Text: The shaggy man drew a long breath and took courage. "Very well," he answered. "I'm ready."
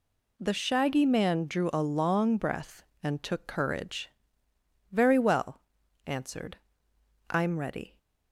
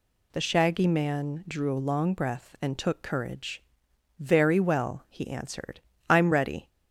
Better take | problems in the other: second | skips "he"; at 5.8 s

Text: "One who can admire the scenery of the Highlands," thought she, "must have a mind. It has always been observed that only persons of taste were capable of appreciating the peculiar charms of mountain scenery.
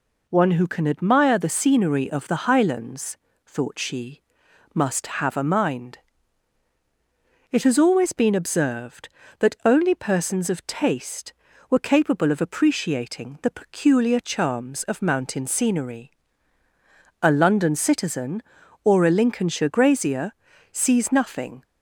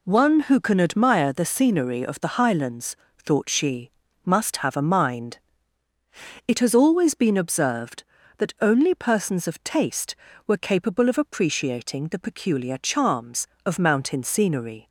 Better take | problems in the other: second | goes on to say "A London citizen or a Lincolnshire grazier sees nothing"; strong; from 17.2 s on; 4.4 s long

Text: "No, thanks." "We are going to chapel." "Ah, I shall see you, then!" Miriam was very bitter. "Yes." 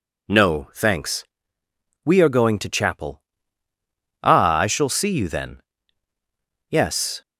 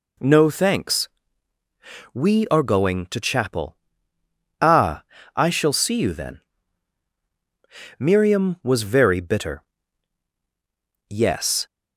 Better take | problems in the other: second | skips "Miriam was very bitter"; at 6.1 s

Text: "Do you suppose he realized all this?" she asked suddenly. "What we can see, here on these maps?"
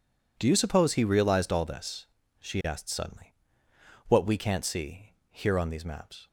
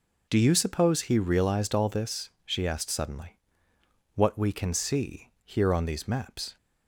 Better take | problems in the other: second | says "can't" for "can"; at 4.3 s

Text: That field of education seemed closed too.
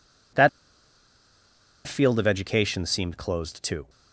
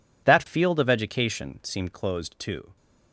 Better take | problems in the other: second | pauses between "That" and "field"; strong; at 0.4 s; 1.3 s long

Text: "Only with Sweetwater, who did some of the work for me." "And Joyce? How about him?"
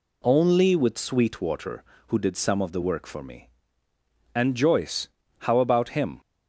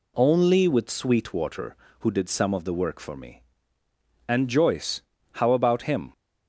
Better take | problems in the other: neither | none

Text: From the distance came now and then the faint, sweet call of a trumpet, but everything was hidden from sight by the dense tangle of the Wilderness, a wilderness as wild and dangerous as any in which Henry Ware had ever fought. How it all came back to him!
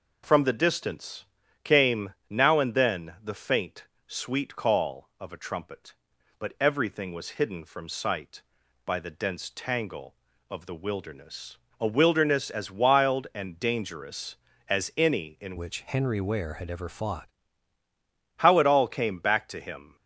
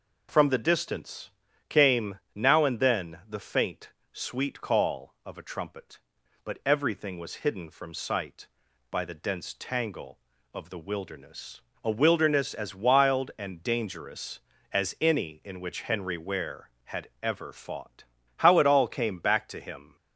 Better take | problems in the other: second | pauses between "distance" and "came"; at 1.2 s; 0.38 s long; also in the second // pauses between "came" and "now"; slight; at 2.1 s; 0.16 s long; slight in the second // changes voice from "which" to "fought"; from 15.5 to 17.2 s; 1.7 s long

